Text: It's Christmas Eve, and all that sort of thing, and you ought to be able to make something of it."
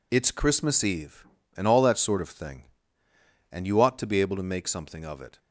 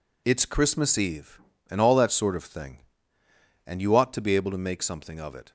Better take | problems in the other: neither | none

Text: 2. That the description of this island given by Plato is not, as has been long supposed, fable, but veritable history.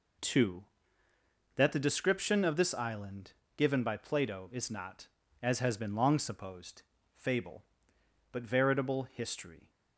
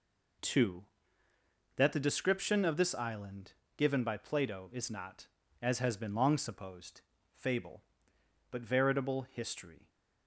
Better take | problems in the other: neither | pauses between "island" and "given"; slight; the same in both

